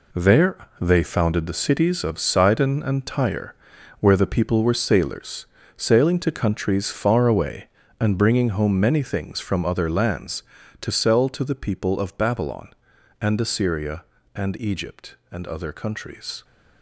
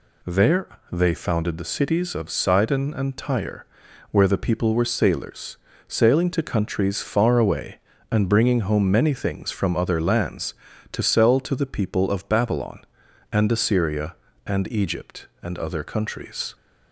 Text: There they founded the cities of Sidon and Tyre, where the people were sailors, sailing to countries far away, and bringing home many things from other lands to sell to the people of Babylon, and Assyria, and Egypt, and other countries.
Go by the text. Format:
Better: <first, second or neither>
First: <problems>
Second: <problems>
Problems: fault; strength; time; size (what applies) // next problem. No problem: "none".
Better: second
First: gets quieter; strong; throughout; 9 dB // pauses between "There" and "they"; slight; at 0.5 s; 0.22 s long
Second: pauses between "There" and "they"; slight; at 0.6 s; 0.22 s long